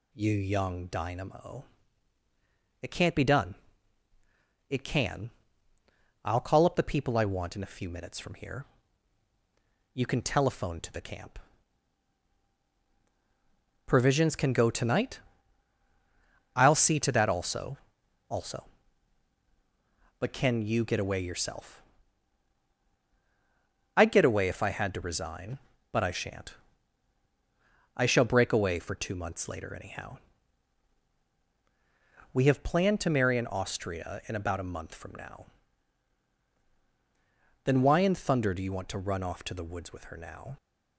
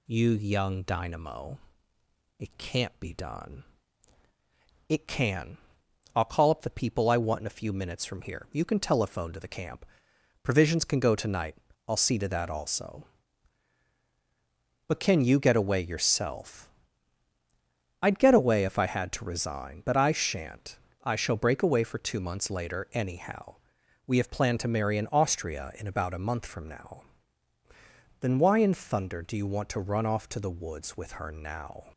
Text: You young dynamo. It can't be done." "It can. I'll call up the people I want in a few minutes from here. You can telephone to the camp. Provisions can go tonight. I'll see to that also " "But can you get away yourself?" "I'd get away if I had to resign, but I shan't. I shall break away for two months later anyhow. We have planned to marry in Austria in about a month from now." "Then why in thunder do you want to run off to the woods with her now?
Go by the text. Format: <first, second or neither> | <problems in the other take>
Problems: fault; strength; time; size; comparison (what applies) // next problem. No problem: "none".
second | says "also" twice; at 18.2 s